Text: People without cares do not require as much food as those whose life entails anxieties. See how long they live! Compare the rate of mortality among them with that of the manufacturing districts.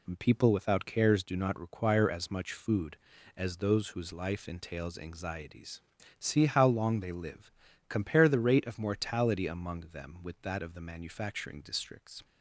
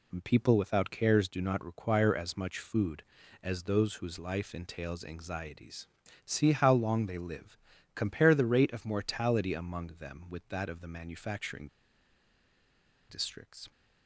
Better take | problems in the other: first | pauses between "manufacturing" and "districts"; strong; at 11.6 s; 1.4 s long

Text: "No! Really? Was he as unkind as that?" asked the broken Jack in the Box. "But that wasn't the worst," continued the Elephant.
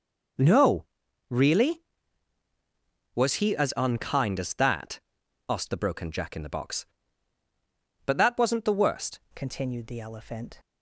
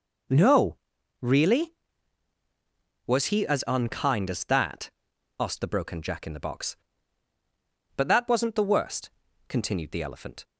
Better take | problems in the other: second | changes voice at "continued"; from 9.3 s on; 1.2 s long

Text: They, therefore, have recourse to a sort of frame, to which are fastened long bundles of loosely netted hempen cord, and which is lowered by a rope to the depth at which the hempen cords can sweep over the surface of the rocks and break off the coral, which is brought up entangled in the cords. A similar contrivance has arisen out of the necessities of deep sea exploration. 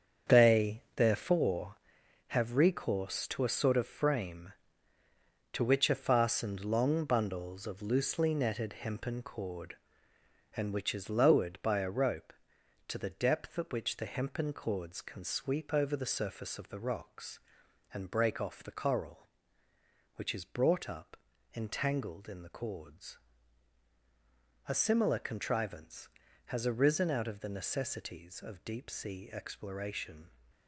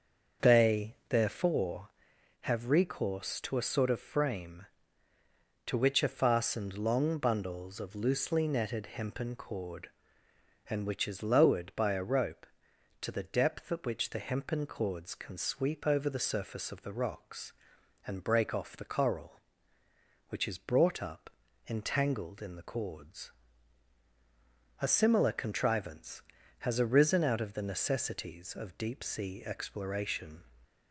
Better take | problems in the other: second | gets quieter; strong; throughout; 9.5 dB // starts louder than the rest; strong; until 1.4 s; 7.5 dB; also in the second // pauses between "up" and "entangled"; at 21.1 s; 0.40 s long; also in the second

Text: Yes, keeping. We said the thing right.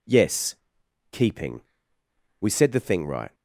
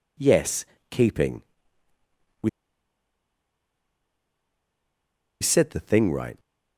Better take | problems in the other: first | pauses between "We" and "said"; strong; at 2.4 s; 2.9 s long

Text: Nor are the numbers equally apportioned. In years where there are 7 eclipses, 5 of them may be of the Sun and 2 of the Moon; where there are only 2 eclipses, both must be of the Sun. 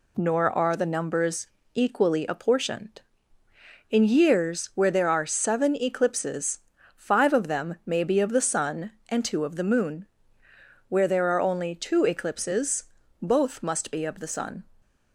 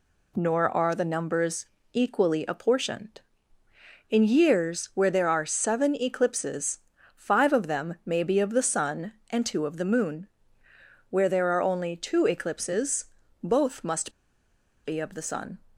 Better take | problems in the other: first | pauses between "numbers" and "equally"; slight; at 1.6 s; 0.28 s long; slight in the first // pauses between "must" and "be"; noticeable; at 14.1 s; 0.74 s long

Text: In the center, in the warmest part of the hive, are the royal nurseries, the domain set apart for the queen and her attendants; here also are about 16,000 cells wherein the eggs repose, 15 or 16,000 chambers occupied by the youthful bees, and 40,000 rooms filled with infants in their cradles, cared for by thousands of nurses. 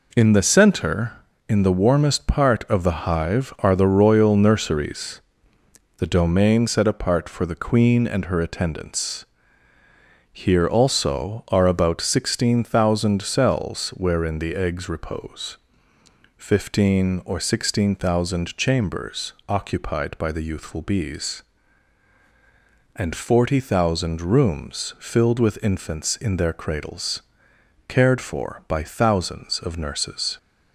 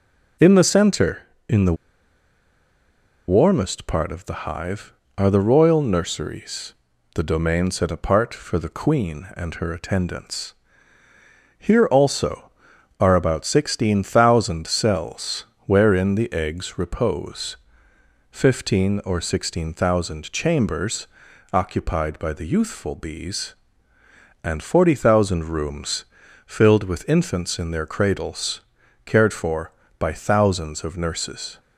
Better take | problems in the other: first | pauses between "the" and "warmest"; strong; at 1.7 s; 1.5 s long // pauses between "cells" and "wherein"; slight; at 15.4 s; 0.22 s long // pauses between "chambers" and "occupied"; noticeable; at 21.0 s; 0.48 s long // pauses between "rooms" and "filled"; at 26.0 s; 0.42 s long

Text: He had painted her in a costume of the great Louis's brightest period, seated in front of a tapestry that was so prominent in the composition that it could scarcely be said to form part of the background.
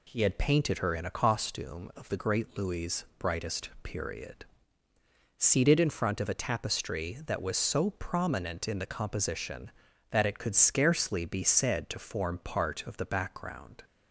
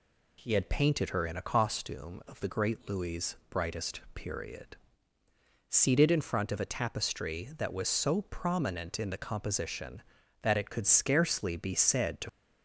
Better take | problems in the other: first | pauses between "brightest" and "period"; slight; at 3.9 s; 0.16 s long; slight in the first // stops before "form part of the background"; at 12.2 s

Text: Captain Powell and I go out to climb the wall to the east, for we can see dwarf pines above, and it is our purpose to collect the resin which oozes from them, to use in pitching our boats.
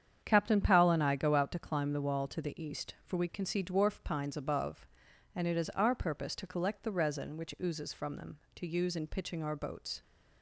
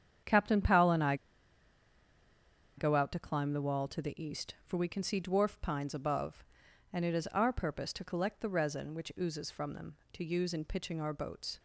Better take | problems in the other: first | starts louder than the rest; strong; until 2.8 s; 8.5 dB; strong in the first // pauses between "I" and "go"; strong; at 1.1 s; 1.6 s long

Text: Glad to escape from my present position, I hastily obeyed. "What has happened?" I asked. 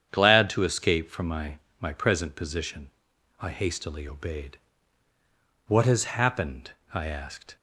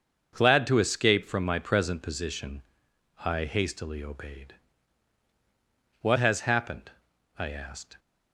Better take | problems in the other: second | starts louder than the rest; strong; until 1.1 s; 8.5 dB; also in the second // says "my" twice; at 1.7 s

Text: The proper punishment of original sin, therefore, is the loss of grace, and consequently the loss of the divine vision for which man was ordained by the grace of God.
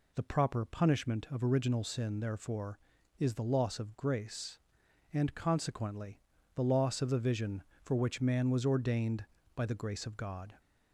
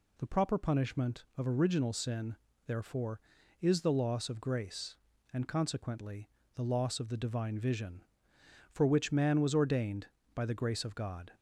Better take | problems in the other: second | pauses between "consequently" and "the"; slight; at 6.2 s; 0.34 s long; slight in the second // skips "divine"; at 7.1 s

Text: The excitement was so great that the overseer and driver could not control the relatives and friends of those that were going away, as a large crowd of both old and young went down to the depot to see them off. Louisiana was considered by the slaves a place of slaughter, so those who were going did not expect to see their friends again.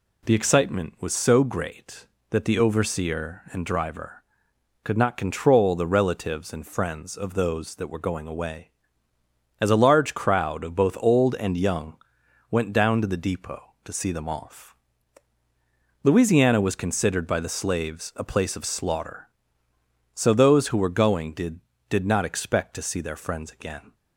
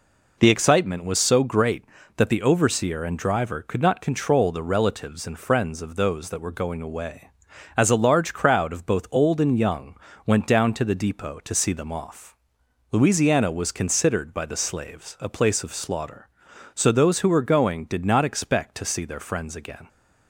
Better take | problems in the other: second | pauses between "young" and "went"; noticeable; at 11.9 s; 0.52 s long; slight in the second // says "did" twice; at 21.8 s

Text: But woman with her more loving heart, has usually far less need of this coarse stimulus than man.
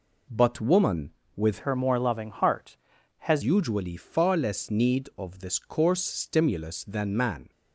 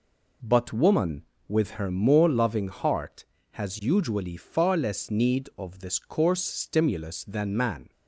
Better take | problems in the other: second | changes voice from "her" to "has"; from 1.6 to 3.4 s; 1.8 s long

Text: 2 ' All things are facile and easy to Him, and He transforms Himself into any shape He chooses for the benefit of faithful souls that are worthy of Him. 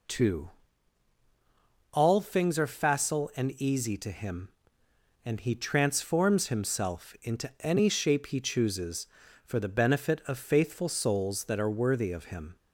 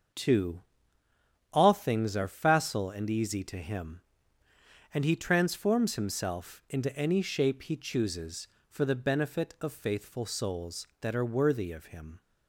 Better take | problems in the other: neither | none

